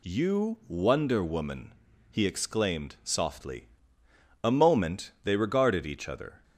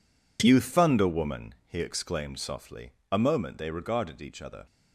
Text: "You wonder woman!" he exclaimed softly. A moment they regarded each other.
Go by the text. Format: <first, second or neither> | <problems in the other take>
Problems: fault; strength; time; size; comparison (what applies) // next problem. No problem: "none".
first | says "thunder" for "wonder"; at 0.5 s